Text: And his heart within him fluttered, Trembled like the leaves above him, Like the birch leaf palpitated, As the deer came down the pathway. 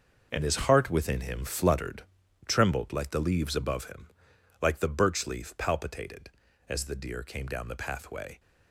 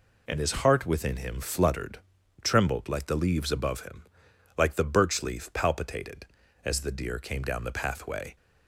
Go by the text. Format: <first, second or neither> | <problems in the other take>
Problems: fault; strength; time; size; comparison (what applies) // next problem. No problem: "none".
second | gets quieter; strong; throughout; 10 dB